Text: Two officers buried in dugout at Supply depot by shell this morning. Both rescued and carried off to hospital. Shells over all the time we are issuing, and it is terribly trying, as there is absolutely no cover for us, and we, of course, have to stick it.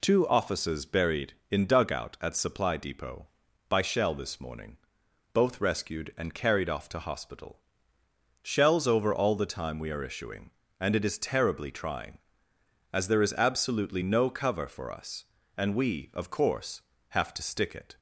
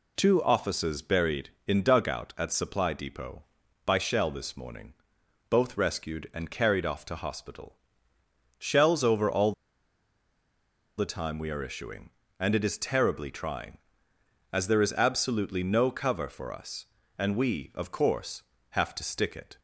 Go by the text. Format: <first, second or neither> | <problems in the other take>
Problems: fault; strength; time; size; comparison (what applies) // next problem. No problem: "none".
first | pauses between "all" and "the"; strong; at 9.5 s; 1.4 s long